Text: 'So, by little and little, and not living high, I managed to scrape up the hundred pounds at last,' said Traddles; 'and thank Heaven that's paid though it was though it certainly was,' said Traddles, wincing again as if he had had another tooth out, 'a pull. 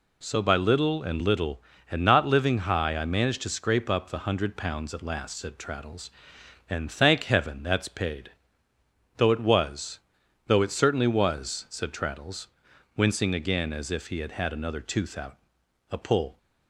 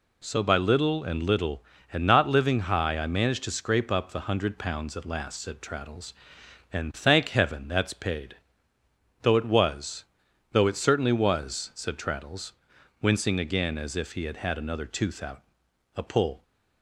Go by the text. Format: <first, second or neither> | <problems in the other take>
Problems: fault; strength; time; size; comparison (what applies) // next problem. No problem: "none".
neither | pauses between "paid" and "though"; noticeable; the same in both // pauses between "was" and "though"; noticeable; the same in both